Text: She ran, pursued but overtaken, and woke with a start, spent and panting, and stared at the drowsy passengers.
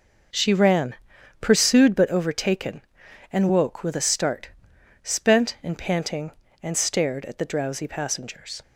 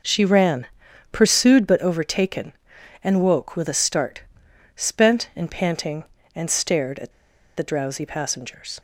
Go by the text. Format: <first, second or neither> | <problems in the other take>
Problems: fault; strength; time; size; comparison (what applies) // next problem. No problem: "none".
first | starts louder than the rest; until 1.5 s; 6 dB; noticeable in the first // pauses between "at" and "the"; at 7.1 s; 0.45 s long